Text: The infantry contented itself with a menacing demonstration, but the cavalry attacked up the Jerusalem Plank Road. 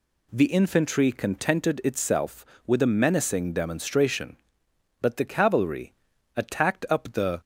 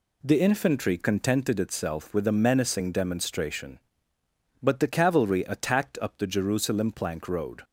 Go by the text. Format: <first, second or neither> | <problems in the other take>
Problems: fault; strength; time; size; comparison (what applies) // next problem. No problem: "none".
second | pauses between "cavalry" and "attacked"; at 5.9 s; 0.42 s long // stops before "Jerusalem Plank Road"; at 7.3 s